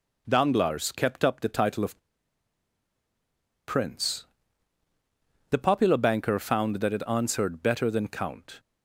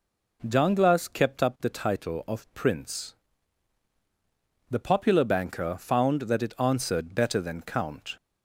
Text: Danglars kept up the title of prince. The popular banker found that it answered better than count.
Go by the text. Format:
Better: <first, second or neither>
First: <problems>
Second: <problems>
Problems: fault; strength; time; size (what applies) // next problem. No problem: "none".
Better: second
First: pauses between "of" and "prince"; strong; at 1.9 s; 1.6 s long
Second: none